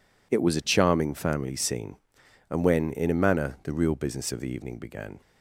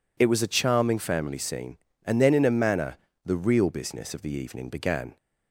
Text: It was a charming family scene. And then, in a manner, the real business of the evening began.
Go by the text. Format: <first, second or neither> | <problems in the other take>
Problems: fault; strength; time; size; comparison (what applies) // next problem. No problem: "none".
second | says "when" for "then"; at 2.6 s